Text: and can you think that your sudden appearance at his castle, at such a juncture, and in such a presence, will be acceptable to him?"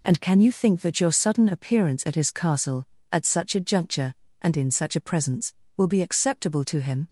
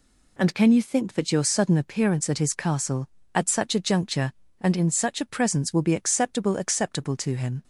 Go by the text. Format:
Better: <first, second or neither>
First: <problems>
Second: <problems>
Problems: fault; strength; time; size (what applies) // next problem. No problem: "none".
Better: first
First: none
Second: says "acceptable" twice; at 6.5 s